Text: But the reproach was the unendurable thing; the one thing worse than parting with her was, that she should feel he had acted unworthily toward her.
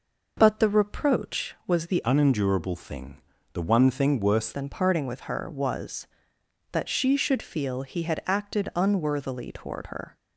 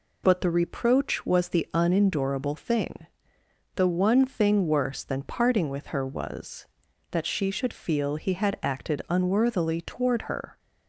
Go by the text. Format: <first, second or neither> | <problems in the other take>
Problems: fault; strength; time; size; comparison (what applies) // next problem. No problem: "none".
second | changes voice from "unendurable" to "worse"; from 2.0 to 4.5 s; 2.5 s long